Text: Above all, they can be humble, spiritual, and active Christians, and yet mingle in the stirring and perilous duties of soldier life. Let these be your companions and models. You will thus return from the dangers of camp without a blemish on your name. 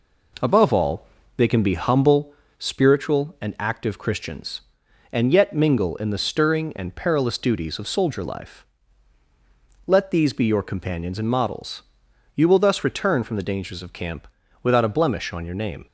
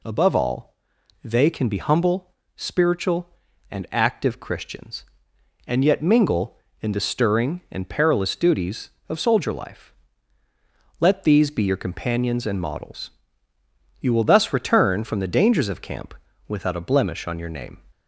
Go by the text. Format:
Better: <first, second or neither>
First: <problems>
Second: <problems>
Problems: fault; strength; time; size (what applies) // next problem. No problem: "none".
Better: neither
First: pauses between "camp" and "without"; slight; at 14.2 s; 0.36 s long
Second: pauses between "camp" and "without"; slight; at 16.1 s; 0.34 s long